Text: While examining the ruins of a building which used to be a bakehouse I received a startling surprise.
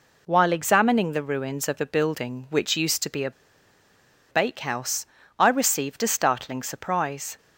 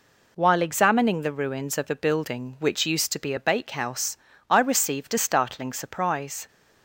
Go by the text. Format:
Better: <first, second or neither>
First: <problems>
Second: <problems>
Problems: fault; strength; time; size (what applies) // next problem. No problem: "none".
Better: second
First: pauses between "a" and "bakehouse"; at 3.3 s; 1.0 s long // pauses between "bakehouse" and "I"; slight; at 5.0 s; 0.34 s long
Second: pauses between "bakehouse" and "I"; slight; at 4.1 s; 0.34 s long